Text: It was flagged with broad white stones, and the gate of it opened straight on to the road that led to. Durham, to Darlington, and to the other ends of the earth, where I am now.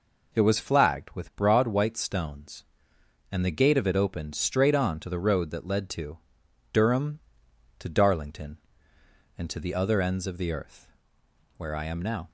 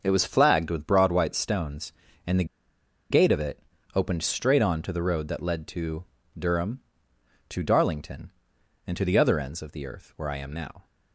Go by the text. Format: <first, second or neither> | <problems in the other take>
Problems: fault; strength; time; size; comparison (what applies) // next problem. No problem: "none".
first | starts louder than the rest; until 1.0 s; 6.5 dB // pauses between "the" and "gate"; noticeable; at 2.4 s; 0.66 s long // pauses between "it" and "opened"; slight; at 3.5 s; 0.36 s long